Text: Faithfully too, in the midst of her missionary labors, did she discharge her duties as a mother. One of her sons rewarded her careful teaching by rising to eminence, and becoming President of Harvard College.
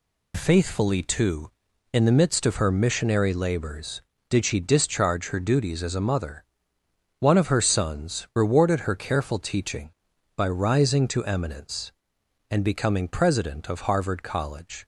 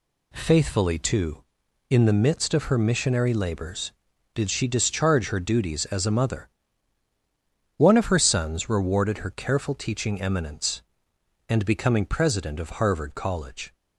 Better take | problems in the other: first | skips "by rising to"; at 10.2 s

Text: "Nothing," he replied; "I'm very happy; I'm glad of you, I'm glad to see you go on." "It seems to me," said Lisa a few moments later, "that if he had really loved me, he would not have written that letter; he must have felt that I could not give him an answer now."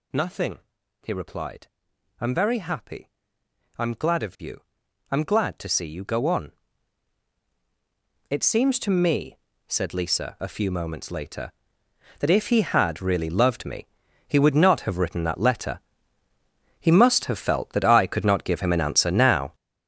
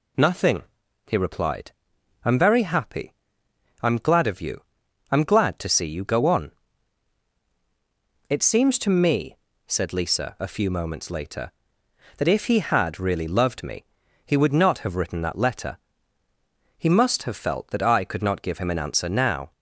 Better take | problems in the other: second | gets louder; strong; throughout; 9.5 dB

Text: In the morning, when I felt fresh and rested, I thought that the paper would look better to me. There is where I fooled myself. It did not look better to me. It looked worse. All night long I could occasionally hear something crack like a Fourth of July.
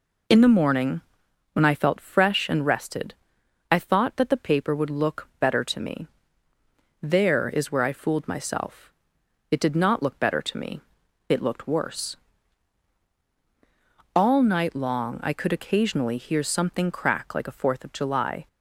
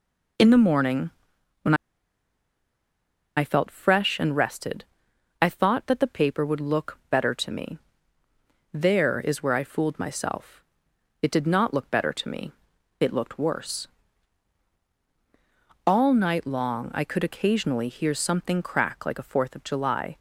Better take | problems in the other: first | pauses between "when" and "I"; strong; at 1.7 s; 1.6 s long

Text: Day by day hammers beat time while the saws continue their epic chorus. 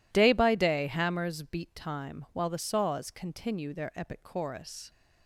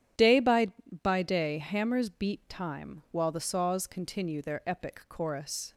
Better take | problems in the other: first | starts louder than the rest; strong; until 1.5 s; 11 dB // says "by" twice; at 1.0 s

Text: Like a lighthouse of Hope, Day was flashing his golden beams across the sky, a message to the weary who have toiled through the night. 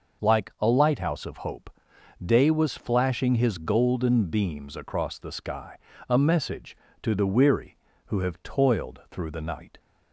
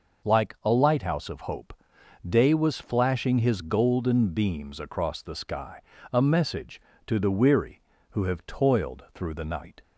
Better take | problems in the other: neither | none

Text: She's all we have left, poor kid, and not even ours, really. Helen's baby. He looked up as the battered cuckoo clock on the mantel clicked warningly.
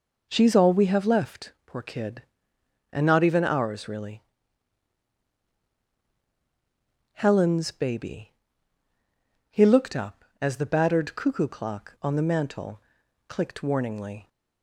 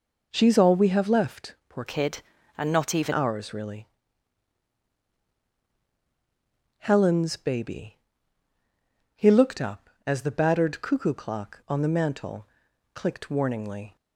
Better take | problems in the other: first | changes voice from "kid" to "even"; from 1.8 to 3.1 s; 1.3 s long // pauses between "mantel" and "clicked"; noticeable; at 12.4 s; 0.48 s long; noticeable in the first

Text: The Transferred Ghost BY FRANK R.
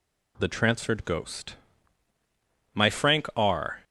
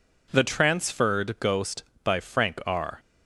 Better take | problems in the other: second | says "My" for "BY"; at 2.7 s

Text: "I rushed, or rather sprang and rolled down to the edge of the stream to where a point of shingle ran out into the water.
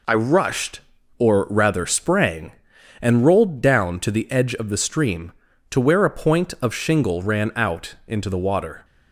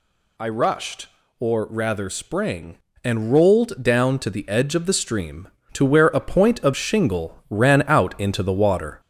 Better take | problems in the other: first | gets louder; slight; throughout; 3.5 dB

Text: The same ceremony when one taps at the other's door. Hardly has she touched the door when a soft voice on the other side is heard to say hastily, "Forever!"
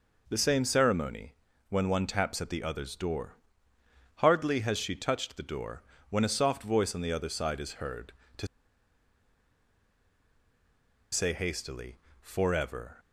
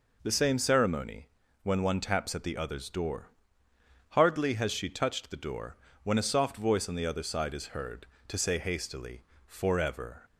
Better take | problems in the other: second | pauses between "ceremony" and "when"; slight; at 1.3 s; 0.34 s long; slight in the second // pauses between "door" and "when"; slight; at 5.8 s; 0.26 s long; slight in the second // pauses between "to" and "say"; strong; at 8.4 s; 2.6 s long

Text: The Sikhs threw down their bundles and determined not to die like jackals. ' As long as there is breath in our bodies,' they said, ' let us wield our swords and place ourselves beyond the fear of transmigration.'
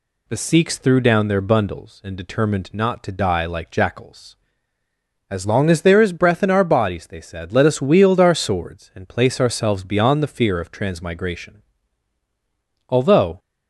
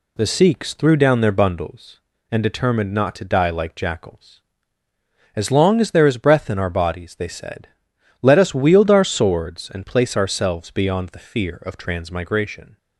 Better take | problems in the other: second | goes on to say "Although"; from 12.8 s on; 0.50 s long

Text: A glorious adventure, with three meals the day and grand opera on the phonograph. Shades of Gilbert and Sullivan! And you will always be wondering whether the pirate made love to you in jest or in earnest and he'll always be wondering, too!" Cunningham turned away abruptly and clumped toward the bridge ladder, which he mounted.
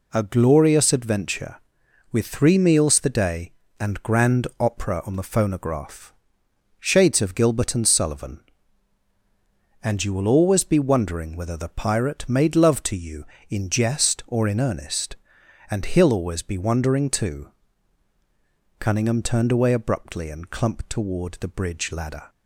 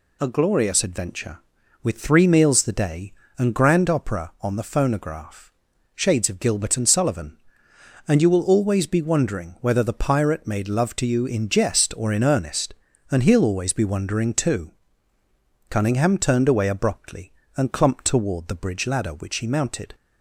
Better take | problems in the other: second | stops before "which he mounted"; at 22.2 s

